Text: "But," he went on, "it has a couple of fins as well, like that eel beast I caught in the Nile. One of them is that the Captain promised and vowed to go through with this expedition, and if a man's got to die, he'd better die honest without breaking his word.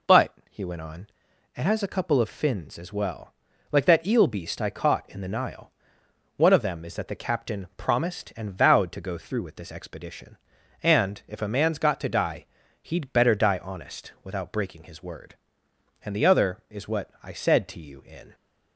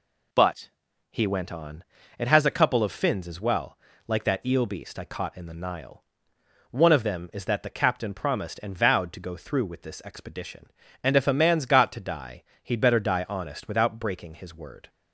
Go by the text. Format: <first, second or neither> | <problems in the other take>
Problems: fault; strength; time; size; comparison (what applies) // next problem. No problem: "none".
second | goes on to say "And the other is what I said to you in"; strong; from 16.0 s on; 2.3 s long